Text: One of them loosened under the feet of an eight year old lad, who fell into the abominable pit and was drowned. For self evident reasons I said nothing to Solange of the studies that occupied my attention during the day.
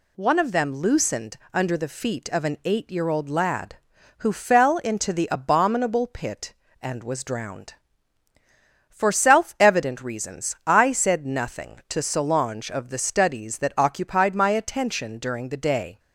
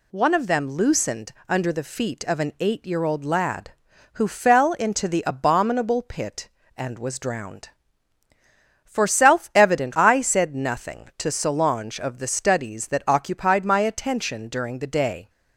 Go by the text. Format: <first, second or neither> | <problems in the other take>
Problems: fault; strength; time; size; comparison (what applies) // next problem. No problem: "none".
first | pauses between "loosened" and "under"; slight; at 1.3 s; 0.16 s long; slight in the first // skips "reasons"; at 9.9 s